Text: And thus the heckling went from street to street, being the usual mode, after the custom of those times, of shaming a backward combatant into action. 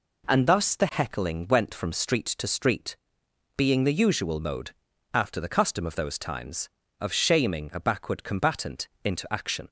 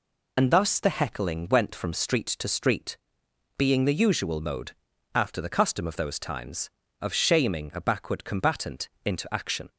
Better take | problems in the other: first | loses the start of "And"; at 0.3 s; 95 ms // pauses between "combatant" and "into"; slight; at 8.8 s; 0.16 s long; slight in the first

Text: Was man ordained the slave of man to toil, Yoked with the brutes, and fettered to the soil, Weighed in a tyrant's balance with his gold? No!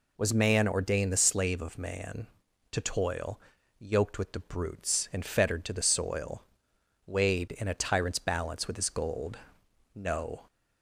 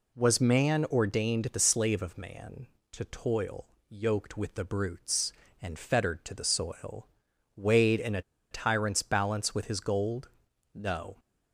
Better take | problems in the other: first | pauses between "a" and "tyrant's"; slight; at 8.2 s; 0.30 s long

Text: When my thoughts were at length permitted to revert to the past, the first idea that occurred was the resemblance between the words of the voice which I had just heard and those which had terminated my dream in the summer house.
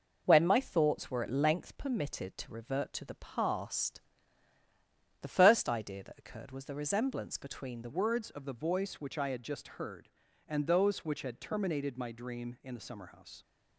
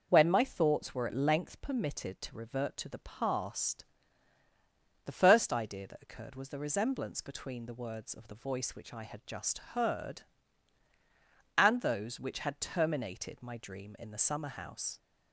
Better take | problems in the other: second | changes voice at "words"; from 7.9 s on; 5.5 s long

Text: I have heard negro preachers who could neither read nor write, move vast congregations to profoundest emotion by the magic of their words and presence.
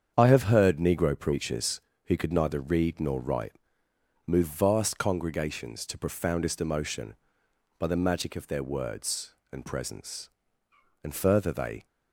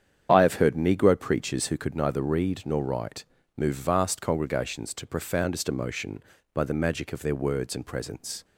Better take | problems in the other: second | starts louder than the rest; strong; until 1.1 s; 8 dB; strong in the second // goes on to say "And further they"; noticeable; from 11.0 s on; 0.84 s long

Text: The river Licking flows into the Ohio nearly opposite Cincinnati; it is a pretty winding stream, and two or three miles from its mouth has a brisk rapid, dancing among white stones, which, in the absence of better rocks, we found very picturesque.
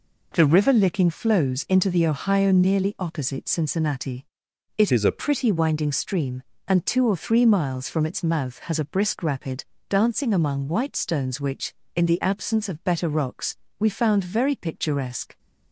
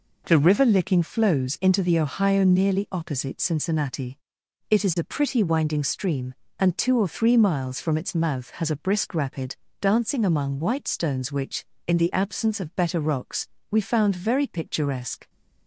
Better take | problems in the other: second | changes voice from "is" to "a"; from 4.9 to 5.2 s; 0.3 s long

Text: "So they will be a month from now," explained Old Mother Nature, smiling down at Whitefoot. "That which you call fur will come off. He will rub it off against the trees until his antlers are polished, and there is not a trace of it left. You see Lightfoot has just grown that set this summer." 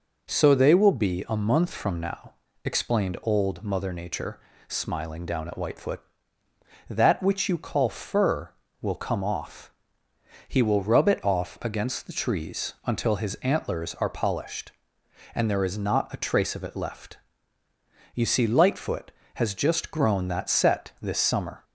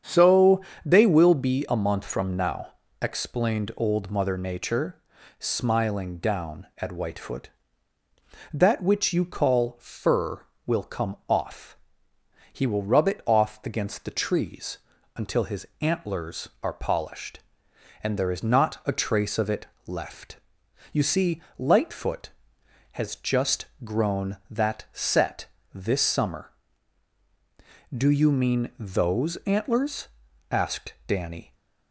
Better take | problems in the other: first | starts louder than the rest; strong; until 1.3 s; 8 dB // pauses between "So" and "they"; slight; at 0.6 s; 0.24 s long // pauses between "trees" and "until"; at 14.7 s; 0.40 s long // pauses between "it" and "left"; slight; at 19.6 s; 0.20 s long // pauses between "see" and "Lightfoot"; slight; at 21.4 s; 0.16 s long // pauses between "just" and "grown"; slight; at 23.6 s; 0.18 s long // pauses between "set" and "this"; slight; at 25.4 s; 0.26 s long // goes on to say "Do you mean those antlers asked Danny"; strong; from 27.9 s on; 3.6 s long

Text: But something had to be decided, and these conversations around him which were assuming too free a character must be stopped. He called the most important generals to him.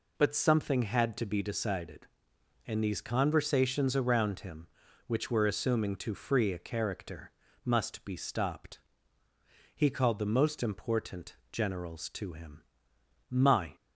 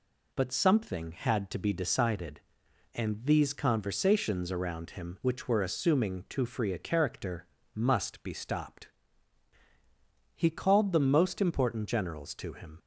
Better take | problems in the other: second | pauses between "character" and "must"; slight; at 7.3 s; 0.32 s long; slight in the second // pauses between "important" and "generals"; slight; at 11.3 s; 0.22 s long // goes on to say "My"; slight; from 13.2 s on; 0.46 s long

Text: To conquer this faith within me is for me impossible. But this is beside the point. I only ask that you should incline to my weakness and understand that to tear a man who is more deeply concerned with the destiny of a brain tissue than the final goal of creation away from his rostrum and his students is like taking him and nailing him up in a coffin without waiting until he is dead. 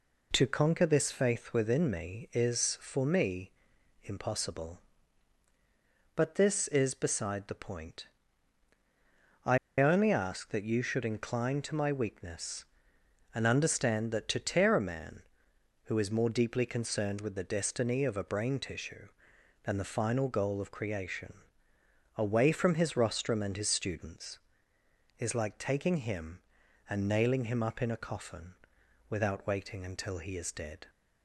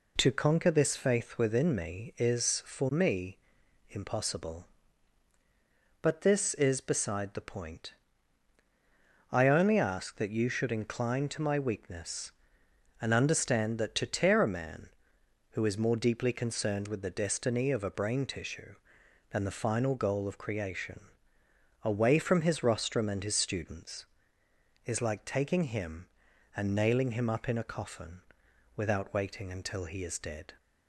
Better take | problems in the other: second | pauses between "me" and "impossible"; noticeable; at 3.5 s; 0.52 s long; noticeable in the second // pauses between "I" and "only"; slight; at 9.5 s; 0.21 s long // pauses between "creation" and "away"; noticeable; at 21.3 s; 0.82 s long; noticeable in the second // pauses between "coffin" and "without"; noticeable; at 28.5 s; 0.56 s long; noticeable in the second

